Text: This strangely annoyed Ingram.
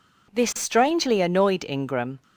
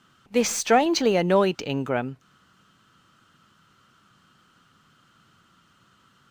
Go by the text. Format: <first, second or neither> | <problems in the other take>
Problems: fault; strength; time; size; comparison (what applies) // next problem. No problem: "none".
first | stays silent after the last word; strong; from 2.1 s on; 4.2 s long